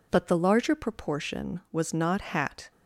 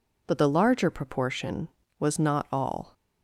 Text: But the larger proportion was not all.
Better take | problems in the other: second | says "hat" for "all"; at 2.2 s

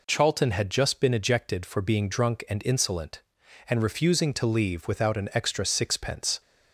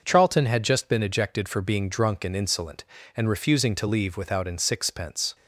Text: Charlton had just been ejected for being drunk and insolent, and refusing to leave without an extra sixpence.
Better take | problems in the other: first | skips "extra"; at 4.5 s

